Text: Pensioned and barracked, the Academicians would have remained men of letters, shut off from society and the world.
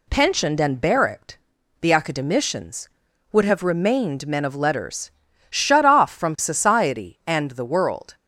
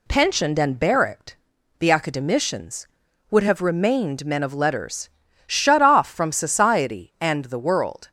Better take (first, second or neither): neither